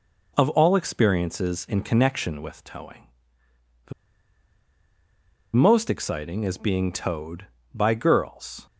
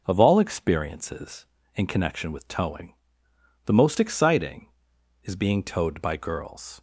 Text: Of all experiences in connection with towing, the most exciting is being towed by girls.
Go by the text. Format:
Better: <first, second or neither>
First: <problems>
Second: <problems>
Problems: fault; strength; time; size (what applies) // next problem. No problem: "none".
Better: second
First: pauses between "the" and "most"; strong; at 3.9 s; 1.6 s long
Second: none